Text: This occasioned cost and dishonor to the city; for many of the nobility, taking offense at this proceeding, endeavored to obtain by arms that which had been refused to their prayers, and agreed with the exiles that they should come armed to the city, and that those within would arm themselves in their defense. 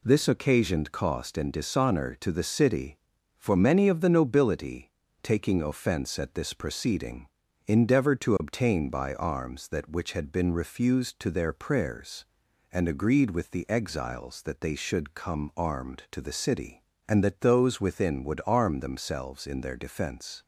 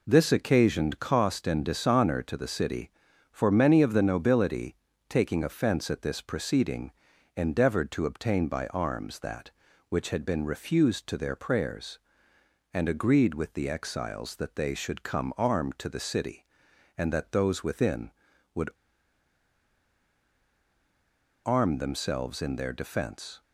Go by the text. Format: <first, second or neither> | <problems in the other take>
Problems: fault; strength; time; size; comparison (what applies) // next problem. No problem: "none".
first | pauses between "would" and "arm"; strong; at 18.6 s; 2.7 s long